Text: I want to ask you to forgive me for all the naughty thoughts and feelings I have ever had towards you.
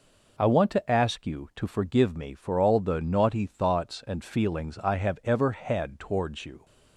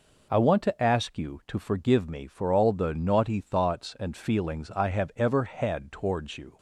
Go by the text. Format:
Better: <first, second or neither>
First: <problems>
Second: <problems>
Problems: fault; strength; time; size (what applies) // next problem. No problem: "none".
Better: neither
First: none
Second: none